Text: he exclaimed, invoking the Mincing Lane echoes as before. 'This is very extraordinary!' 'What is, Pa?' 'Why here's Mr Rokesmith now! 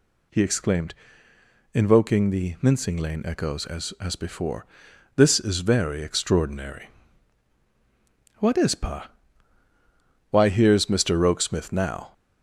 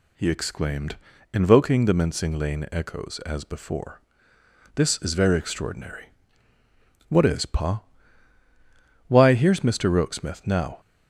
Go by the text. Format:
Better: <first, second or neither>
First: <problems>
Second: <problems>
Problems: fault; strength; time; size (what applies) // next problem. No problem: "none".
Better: second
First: says "as" twice; at 4.0 s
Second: none